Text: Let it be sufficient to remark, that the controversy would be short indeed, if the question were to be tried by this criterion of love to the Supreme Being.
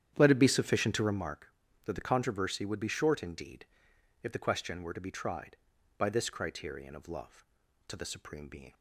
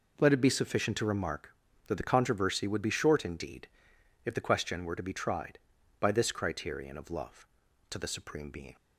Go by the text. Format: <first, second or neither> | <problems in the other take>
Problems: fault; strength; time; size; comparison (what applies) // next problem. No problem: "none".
second | starts louder than the rest; strong; until 1.2 s; 9.5 dB